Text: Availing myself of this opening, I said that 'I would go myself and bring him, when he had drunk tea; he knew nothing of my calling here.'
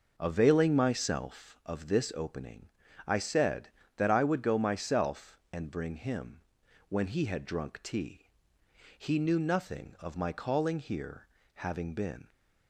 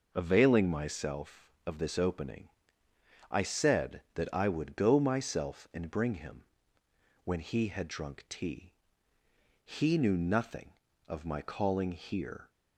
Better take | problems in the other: second | goes on to say "Having been"; noticeable; from 11.5 s on; 0.72 s long

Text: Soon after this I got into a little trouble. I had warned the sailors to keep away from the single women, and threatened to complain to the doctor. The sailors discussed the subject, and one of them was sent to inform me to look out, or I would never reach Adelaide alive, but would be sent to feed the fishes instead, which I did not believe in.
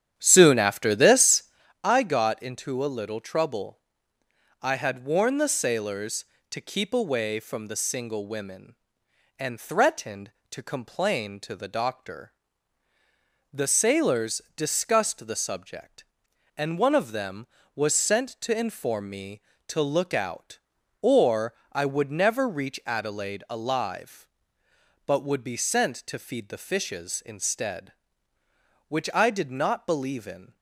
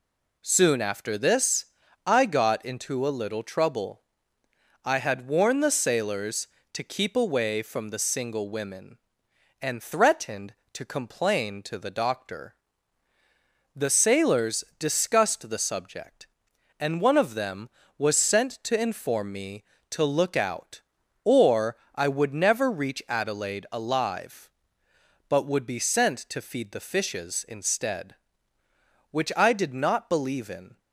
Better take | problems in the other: second | starts louder than the rest; strong; until 1.7 s; 9.5 dB // pauses between "this" and "I"; at 1.4 s; 0.40 s long; also in the second // pauses between "sailors" and "discussed"; slight; at 14.4 s; 0.16 s long; slight in the second // pauses between "or" and "I"; slight; at 21.5 s; 0.20 s long; slight in the second

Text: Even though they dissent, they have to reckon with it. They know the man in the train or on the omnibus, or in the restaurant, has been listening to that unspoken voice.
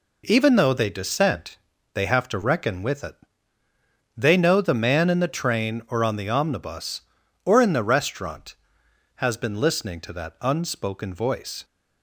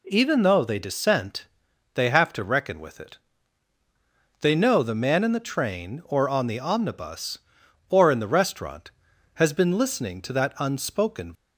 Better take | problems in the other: first | stops before "voice"; at 11.3 s

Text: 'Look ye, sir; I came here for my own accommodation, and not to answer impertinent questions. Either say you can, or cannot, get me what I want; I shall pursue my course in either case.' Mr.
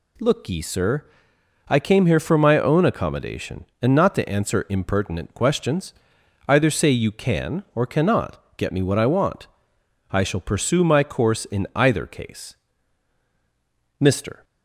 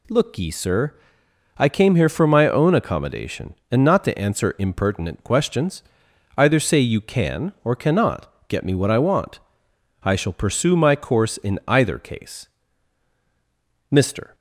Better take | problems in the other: neither | none

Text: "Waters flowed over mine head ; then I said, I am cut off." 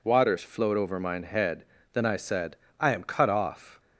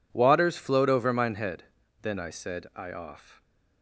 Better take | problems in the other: first | skips "am cut"; at 2.9 s

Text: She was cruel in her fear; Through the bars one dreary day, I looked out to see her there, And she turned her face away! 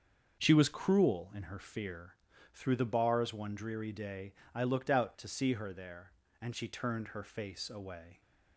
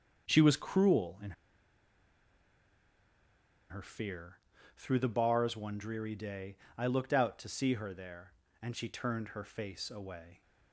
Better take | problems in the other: first | starts louder than the rest; until 1.3 s; 6.5 dB; also in the first // pauses between "in" and "her"; strong; at 1.3 s; 2.3 s long

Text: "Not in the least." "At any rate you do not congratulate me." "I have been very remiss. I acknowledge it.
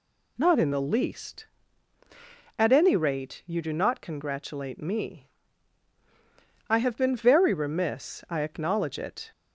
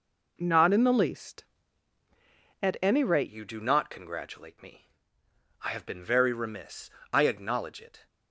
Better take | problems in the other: first | changes voice at "you"; from 3.2 s on; 4.8 s long

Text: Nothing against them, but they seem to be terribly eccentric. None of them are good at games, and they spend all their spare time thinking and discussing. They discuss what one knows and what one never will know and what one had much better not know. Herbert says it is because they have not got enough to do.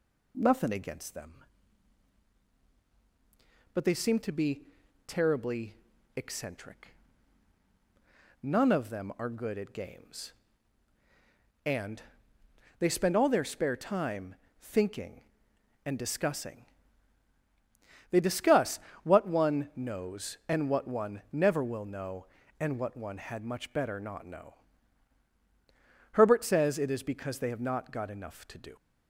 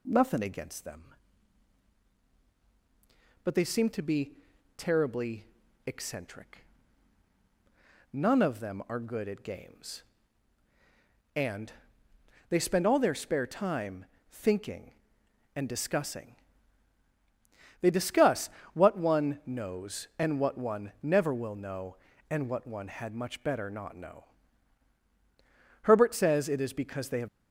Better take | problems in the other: first | pauses between "be" and "terribly"; at 4.3 s; 0.42 s long; also in the first // pauses between "terribly" and "eccentric"; at 5.4 s; 0.38 s long; also in the first // pauses between "and" and "they"; noticeable; at 11.7 s; 0.78 s long; noticeable in the first // pauses between "time" and "thinking"; slight; at 14.0 s; 0.26 s long; slight in the first // pauses between "discuss" and "what"; slight; at 18.4 s; 0.26 s long; slight in the first // stops before "not got enough to do"; at 27.2 s

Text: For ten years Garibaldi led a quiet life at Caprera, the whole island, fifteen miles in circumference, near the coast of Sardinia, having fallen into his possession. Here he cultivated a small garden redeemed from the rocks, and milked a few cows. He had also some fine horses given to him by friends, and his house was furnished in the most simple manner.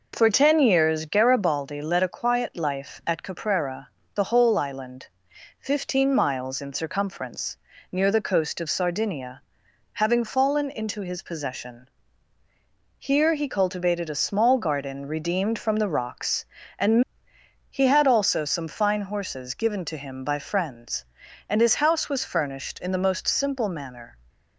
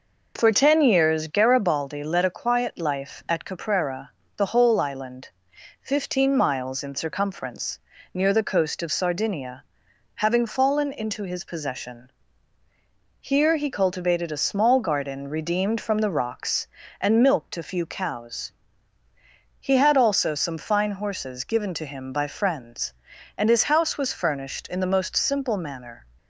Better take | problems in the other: second | skips "milked a few cows"; at 17.3 s

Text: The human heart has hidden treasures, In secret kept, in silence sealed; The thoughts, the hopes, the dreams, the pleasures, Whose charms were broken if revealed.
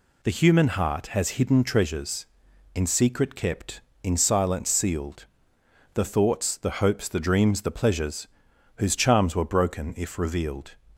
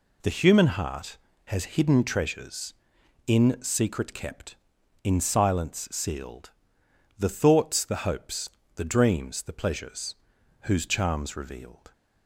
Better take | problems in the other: first | skips "were broken if"; at 11.3 s

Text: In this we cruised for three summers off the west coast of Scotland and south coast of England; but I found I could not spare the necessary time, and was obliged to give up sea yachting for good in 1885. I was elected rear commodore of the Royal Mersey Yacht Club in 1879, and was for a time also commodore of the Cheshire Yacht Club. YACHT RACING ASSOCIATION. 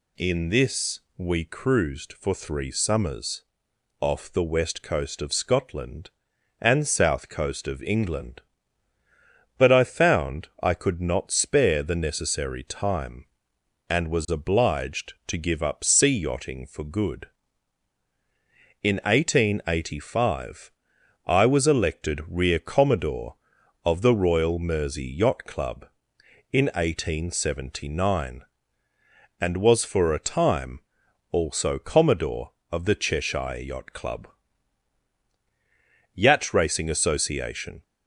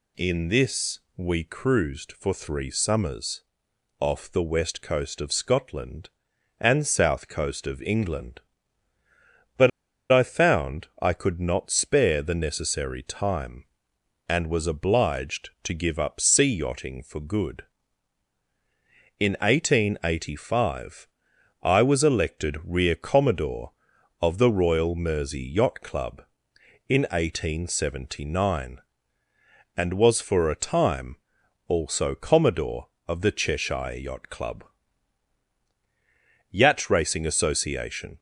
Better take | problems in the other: first | pauses between "this" and "we"; slight; at 0.9 s; 0.18 s long; slight in the first // pauses between "summers" and "off"; noticeable; at 3.4 s; 0.56 s long; noticeable in the first // pauses between "but" and "I"; at 9.6 s; 0.42 s long // pauses between "found" and "I"; slight; at 10.8 s; 0.16 s long; slight in the first // pauses between "time" and "also"; noticeable; at 31.1 s; 0.50 s long; noticeable in the first

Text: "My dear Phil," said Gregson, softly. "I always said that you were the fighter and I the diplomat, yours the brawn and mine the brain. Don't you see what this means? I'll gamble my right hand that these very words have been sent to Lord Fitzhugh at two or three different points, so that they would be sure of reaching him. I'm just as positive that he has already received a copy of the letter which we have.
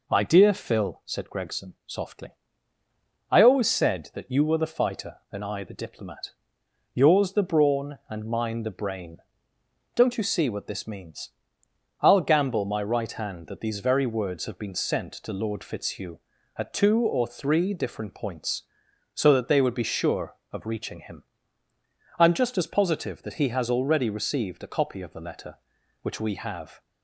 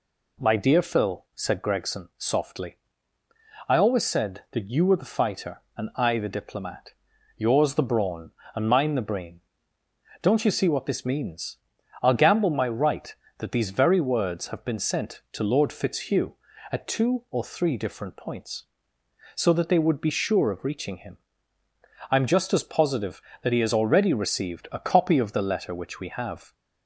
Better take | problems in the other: first | skips "hand"; at 13.2 s

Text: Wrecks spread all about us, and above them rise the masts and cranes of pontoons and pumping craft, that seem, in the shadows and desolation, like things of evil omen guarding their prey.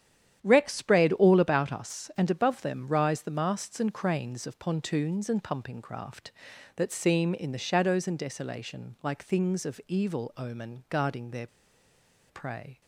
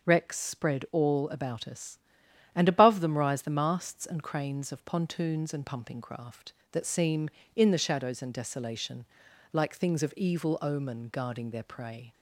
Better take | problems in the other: second | starts louder than the rest; strong; until 1.4 s; 10 dB // pauses between "their" and "prey"; noticeable; at 11.4 s; 0.83 s long

